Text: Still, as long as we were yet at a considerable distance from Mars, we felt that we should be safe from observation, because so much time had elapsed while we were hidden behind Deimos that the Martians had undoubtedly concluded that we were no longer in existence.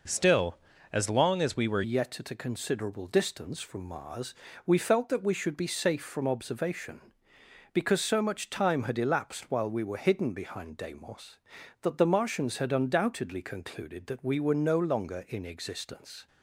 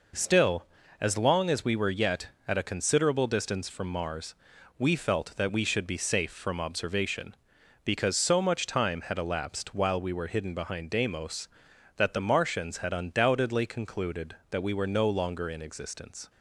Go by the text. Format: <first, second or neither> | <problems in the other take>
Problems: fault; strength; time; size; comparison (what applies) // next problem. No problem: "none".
second | changes voice at "yet"; from 1.8 s on; 14.4 s long